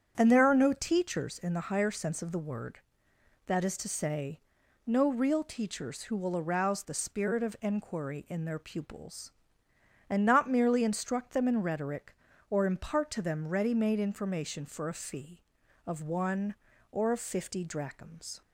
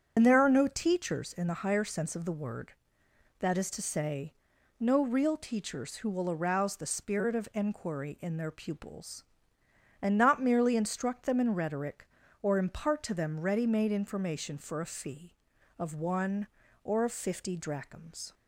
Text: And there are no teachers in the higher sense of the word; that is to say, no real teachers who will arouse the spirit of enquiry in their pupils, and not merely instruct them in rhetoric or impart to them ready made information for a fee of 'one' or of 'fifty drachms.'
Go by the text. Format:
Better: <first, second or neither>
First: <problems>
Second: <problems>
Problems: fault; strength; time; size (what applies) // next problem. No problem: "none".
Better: first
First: starts louder than the rest; strong; until 1.1 s; 8.5 dB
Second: loses the start of "And"; at 0.1 s; 70 ms // starts louder than the rest; strong; until 1.1 s; 7.5 dB